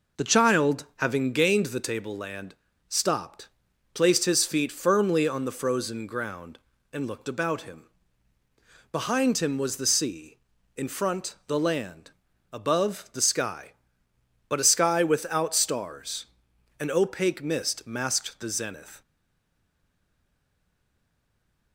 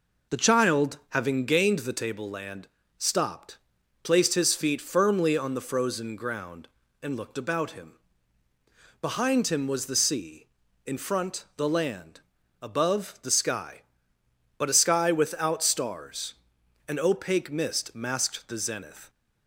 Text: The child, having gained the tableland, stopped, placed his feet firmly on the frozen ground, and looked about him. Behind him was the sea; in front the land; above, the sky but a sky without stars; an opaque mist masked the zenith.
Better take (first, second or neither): second